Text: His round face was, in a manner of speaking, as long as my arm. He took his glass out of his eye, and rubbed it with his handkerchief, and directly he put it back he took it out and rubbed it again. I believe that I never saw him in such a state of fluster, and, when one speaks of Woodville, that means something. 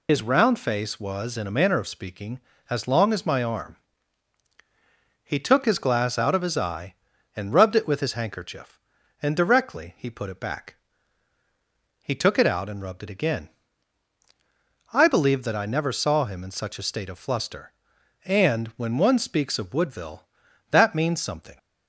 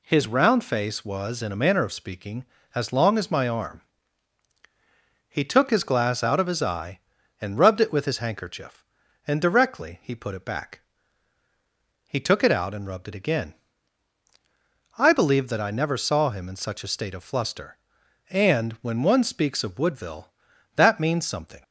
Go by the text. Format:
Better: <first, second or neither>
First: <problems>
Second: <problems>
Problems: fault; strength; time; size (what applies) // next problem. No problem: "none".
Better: second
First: loses the start of "His"; at 0.0 s; 120 ms // pauses between "back" and "he"; strong; at 10.7 s; 1.2 s long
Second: pauses between "back" and "he"; strong; at 10.8 s; 1.2 s long